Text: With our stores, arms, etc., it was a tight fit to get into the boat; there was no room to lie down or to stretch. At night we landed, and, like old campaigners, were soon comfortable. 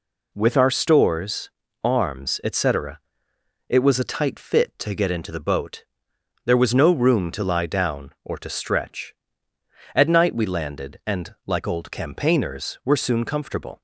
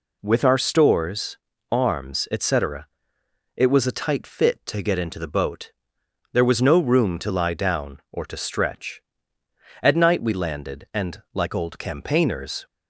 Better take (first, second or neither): first